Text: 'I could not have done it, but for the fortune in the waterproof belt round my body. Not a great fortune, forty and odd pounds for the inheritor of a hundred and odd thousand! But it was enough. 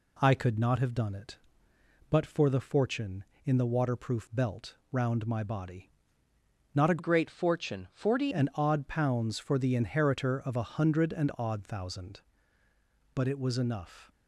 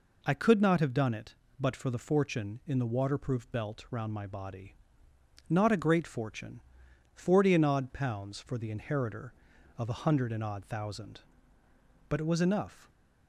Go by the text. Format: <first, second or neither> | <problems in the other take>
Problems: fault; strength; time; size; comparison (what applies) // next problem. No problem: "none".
second | pauses between "belt" and "round"; slight; at 4.7 s; 0.16 s long // changes voice from "great" to "forty"; from 6.9 to 8.3 s; 1.4 s long